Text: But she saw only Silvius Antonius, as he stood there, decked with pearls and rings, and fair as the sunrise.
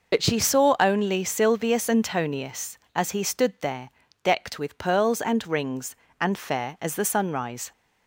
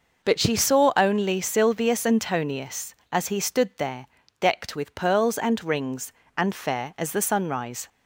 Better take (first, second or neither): second